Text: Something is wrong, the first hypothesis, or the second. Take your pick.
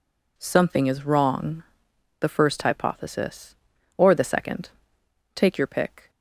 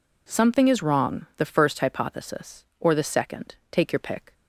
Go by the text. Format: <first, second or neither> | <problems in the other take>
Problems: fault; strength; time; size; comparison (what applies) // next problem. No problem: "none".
neither | none